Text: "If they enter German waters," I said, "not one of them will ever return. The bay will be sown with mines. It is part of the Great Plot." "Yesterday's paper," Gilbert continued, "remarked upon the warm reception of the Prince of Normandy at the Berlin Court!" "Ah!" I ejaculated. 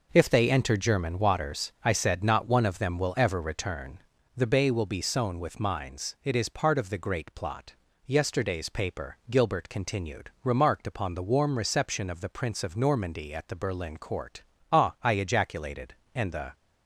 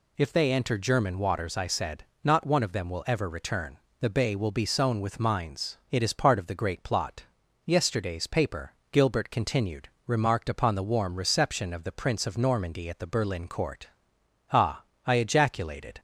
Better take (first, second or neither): second